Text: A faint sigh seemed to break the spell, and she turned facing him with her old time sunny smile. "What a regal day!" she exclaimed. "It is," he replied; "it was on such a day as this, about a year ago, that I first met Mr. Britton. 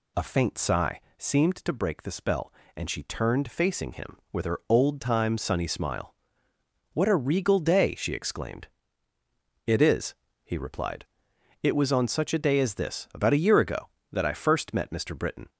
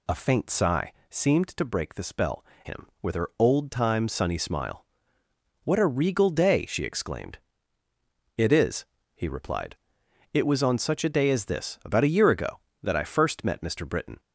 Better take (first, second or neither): first